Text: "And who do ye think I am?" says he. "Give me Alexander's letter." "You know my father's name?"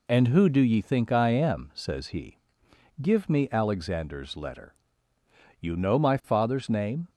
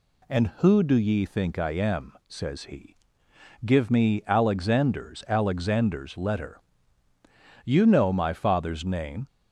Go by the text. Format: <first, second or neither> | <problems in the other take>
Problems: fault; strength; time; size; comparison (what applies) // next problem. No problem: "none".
first | says "Alexander's" twice; at 5.2 s